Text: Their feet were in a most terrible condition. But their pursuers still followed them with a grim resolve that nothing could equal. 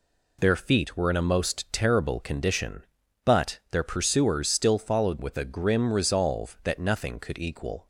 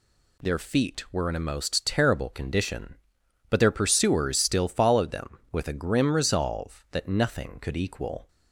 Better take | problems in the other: second | skips "them"; at 5.2 s

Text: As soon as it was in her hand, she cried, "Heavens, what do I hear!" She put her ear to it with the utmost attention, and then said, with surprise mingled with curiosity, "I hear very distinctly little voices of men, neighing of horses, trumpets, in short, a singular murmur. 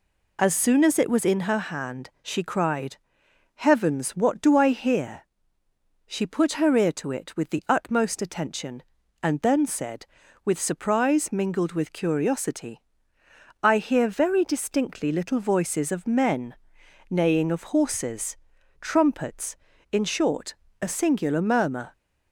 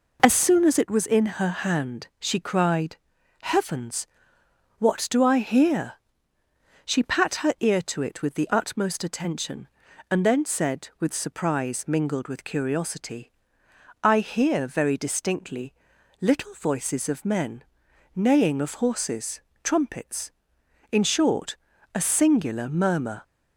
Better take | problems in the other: first | says "pat" for "put"; at 7.0 s // pauses between "distinctly" and "little"; noticeable; at 15.7 s; 0.48 s long

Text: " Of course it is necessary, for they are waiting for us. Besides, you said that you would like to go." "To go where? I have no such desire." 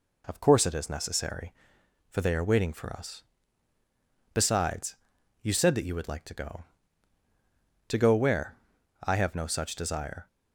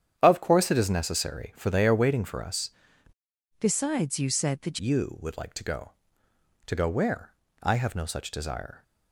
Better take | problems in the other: first | starts louder than the rest; strong; until 1.1 s; 9 dB // changes voice from "Besides" to "that"; from 3.5 to 4.7 s; 1.2 s long

